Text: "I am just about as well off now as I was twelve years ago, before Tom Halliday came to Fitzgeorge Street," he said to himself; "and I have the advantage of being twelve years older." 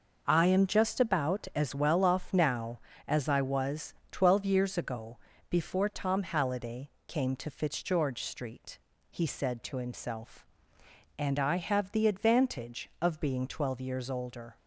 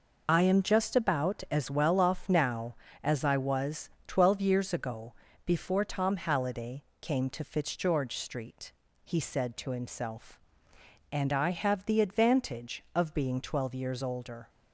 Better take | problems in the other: first | loses the start of "I"; at 0.2 s; 70 ms // pauses between "was" and "twelve"; slight; at 3.8 s; 0.16 s long; slight in the first // pauses between "Halliday" and "came"; slight; at 6.8 s; 0.16 s long; slight in the first

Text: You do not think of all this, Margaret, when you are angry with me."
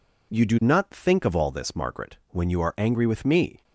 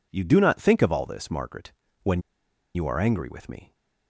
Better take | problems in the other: first | pauses between "when" and "you"; noticeable; at 2.2 s; 0.54 s long

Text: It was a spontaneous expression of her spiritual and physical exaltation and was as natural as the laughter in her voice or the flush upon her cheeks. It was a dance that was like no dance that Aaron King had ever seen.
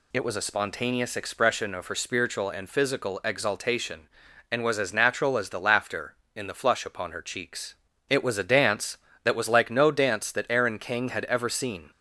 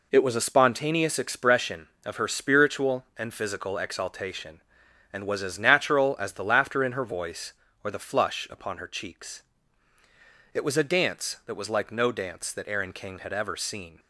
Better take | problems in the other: second | skips "her voice or"; at 6.4 s

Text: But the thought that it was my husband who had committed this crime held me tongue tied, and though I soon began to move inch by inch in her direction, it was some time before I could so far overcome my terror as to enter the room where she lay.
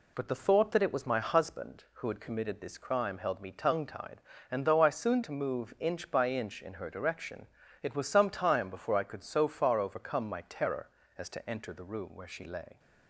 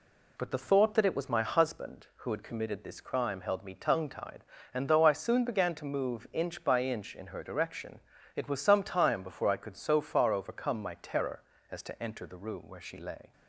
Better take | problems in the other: second | skips "began"; at 5.2 s

